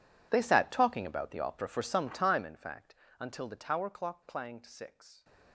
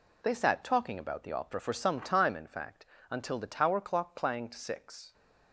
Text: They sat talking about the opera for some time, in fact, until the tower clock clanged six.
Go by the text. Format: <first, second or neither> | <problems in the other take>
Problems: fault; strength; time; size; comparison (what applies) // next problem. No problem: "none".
second | gets quieter; strong; throughout; 20 dB